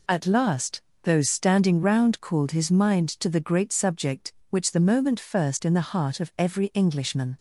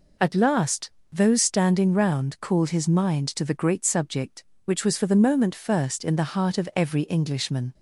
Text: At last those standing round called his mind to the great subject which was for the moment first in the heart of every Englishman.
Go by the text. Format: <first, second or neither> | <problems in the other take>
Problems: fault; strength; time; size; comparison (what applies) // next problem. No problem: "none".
second | pauses between "last" and "those"; slight; at 0.8 s; 0.22 s long; slight in the second // skips "was for"; at 4.7 s